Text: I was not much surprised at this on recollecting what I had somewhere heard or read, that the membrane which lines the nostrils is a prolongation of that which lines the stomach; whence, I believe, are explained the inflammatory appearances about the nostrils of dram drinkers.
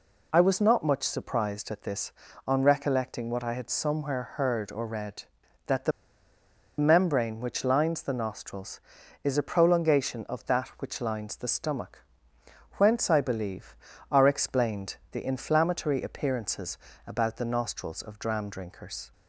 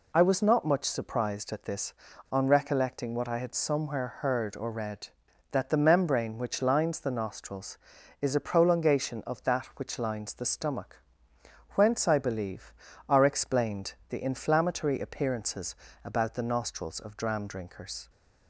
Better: second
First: pauses between "the" and "membrane"; noticeable; at 5.9 s; 0.88 s long // pauses between "explained" and "the"; slight; at 14.9 s; 0.16 s long // pauses between "appearances" and "about"; slight; at 16.7 s; 0.28 s long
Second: pauses between "explained" and "the"; slight; at 13.9 s; 0.16 s long // pauses between "appearances" and "about"; slight; at 15.7 s; 0.28 s long

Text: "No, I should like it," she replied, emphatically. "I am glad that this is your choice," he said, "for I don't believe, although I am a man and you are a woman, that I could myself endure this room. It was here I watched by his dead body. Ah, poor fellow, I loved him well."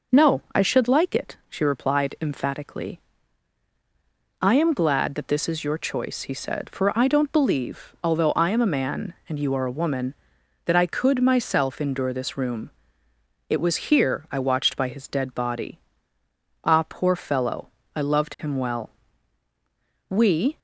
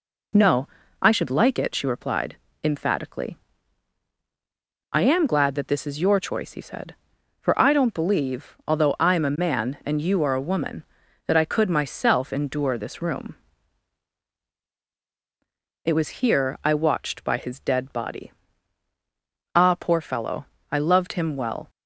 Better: second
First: goes on to say "We"; slight; from 20.1 s on; 0.48 s long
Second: none

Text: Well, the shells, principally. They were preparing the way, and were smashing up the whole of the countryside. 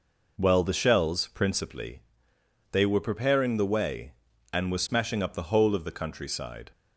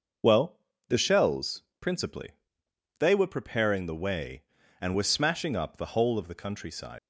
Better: first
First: none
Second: starts louder than the rest; noticeable; until 1.5 s; 6 dB // leaves "countryside" unfinished; at 6.9 s; 110 ms

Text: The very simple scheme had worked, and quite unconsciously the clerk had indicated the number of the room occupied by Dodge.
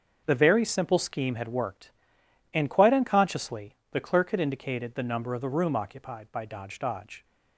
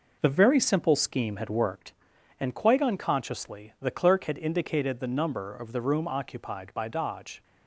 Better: second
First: starts louder than the rest; until 1.2 s; 6.5 dB // pauses between "unconsciously" and "the"; slight; at 3.7 s; 0.16 s long // says "Dodge" twice; at 6.7 s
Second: none

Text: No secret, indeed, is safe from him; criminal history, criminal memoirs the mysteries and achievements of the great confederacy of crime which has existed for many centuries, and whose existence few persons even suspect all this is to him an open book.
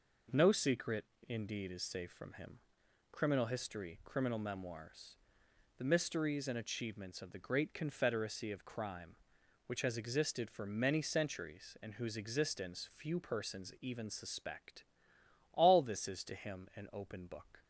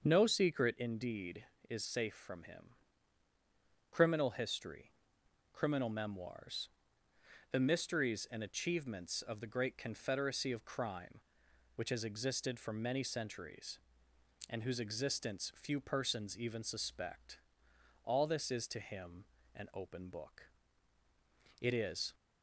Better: first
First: pauses between "memoirs" and "the"; noticeable; at 5.1 s; 0.64 s long // pauses between "suspect" and "all"; noticeable; at 14.8 s; 0.70 s long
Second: starts louder than the rest; until 1.0 s; 6.5 dB // pauses between "memoirs" and "the"; noticeable; at 6.6 s; 0.84 s long // pauses between "suspect" and "all"; noticeable; at 17.3 s; 0.66 s long // pauses between "him" and "an"; slight; at 19.2 s; 0.28 s long // goes on to say "It is"; from 21.5 s on; 0.54 s long

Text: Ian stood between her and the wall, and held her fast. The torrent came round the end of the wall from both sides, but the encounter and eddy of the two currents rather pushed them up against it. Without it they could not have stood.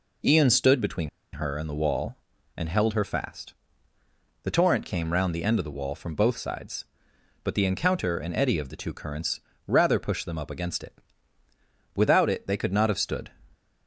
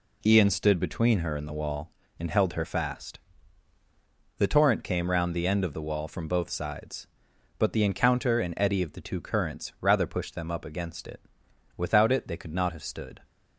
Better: second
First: pauses between "between" and "her"; slight; at 1.0 s; 0.24 s long // pauses between "currents" and "rather"; slight; at 9.3 s; 0.26 s long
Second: none

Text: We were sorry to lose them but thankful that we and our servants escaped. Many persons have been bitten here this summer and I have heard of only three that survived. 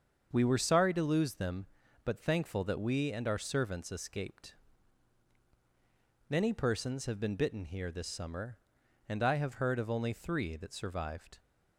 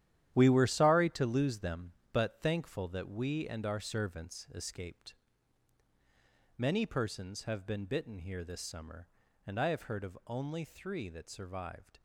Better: first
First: starts louder than the rest; until 1.3 s; 7 dB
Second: gets quieter; strong; throughout; 11 dB // starts louder than the rest; strong; until 1.3 s; 11.5 dB

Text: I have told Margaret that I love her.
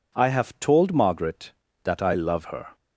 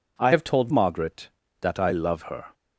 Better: first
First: none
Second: changes voice from "have" to "told"; from 0.3 to 0.7 s; 0.4 s long

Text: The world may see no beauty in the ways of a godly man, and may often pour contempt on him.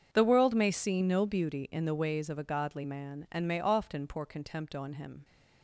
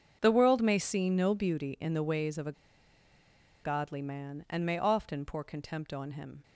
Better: first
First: starts louder than the rest; strong; until 1.1 s; 7 dB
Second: starts louder than the rest; strong; until 1.2 s; 7 dB // pauses between "a" and "godly"; at 2.5 s; 1.1 s long

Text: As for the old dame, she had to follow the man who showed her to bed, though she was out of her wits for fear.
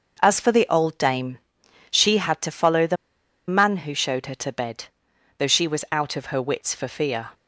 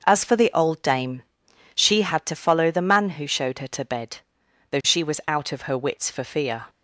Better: second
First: starts louder than the rest; noticeable; until 1.2 s; 6 dB // pauses between "the" and "man"; noticeable; at 2.9 s; 0.53 s long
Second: starts louder than the rest; until 1.0 s; 6 dB

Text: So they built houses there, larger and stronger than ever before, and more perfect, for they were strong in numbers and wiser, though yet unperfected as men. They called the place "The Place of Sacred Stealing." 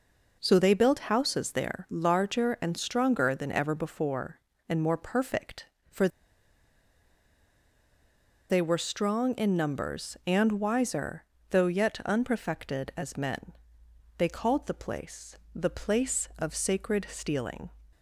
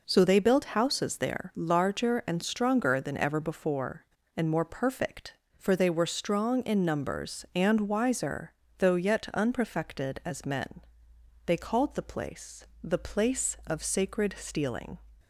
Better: second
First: pauses between "for" and "they"; strong; at 6.0 s; 2.4 s long // pauses between "place" and "The"; slight; at 15.3 s; 0.18 s long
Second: pauses between "place" and "The"; slight; at 12.6 s; 0.18 s long

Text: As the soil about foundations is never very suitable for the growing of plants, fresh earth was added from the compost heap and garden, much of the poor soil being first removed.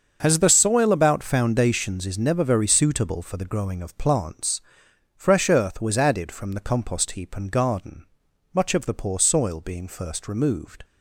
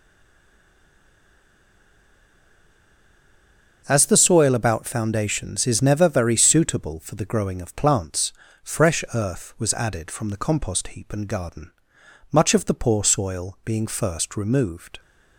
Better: first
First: starts louder than the rest; until 1.2 s; 7 dB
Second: stays silent before the first word; strong; until 3.8 s; 3.8 s long // starts louder than the rest; until 4.8 s; 6.5 dB

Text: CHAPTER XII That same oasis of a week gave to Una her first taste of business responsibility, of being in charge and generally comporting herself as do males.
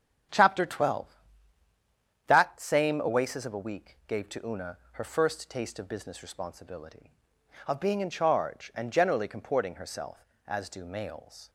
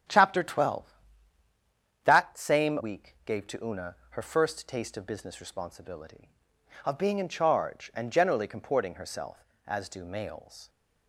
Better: first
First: starts louder than the rest; strong; until 2.5 s; 9.5 dB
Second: starts louder than the rest; strong; until 2.2 s; 10 dB // skips "oasis of a"; at 2.7 s

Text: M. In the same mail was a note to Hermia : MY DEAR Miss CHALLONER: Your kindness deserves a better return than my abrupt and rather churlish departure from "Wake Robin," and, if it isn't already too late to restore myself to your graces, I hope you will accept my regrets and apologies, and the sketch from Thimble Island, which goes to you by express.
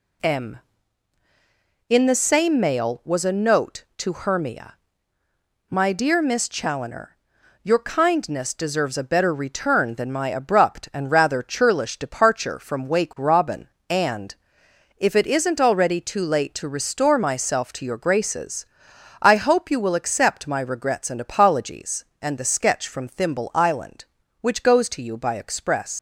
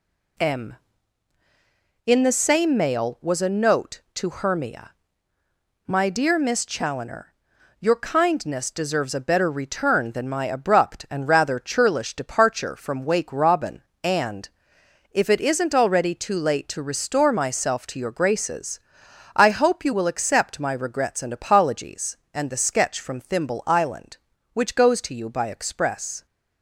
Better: second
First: leaves "express" unfinished; at 25.9 s; 140 ms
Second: none

